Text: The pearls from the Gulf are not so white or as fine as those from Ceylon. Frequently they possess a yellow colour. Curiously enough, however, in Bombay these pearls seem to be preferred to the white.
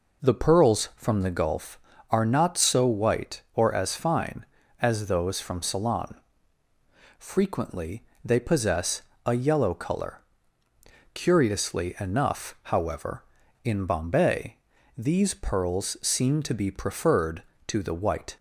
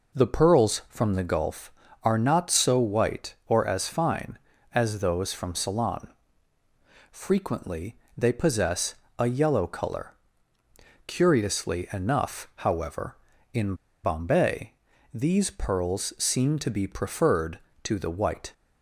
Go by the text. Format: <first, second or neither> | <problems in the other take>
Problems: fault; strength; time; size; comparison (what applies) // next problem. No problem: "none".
first | pauses between "Frequently" and "they"; slight; at 7.9 s; 0.20 s long; slight in the first // pauses between "possess" and "a"; slight; at 8.9 s; 0.24 s long; slight in the first // pauses between "in" and "Bombay"; slight; at 13.7 s; 0.30 s long // pauses between "Bombay" and "these"; at 14.7 s; 0.40 s long; also in the first